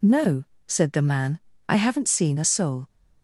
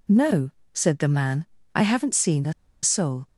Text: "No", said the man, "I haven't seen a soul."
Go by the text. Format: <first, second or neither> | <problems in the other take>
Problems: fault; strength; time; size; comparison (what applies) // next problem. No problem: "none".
first | pauses between "a" and "soul"; slight; at 2.5 s; 0.29 s long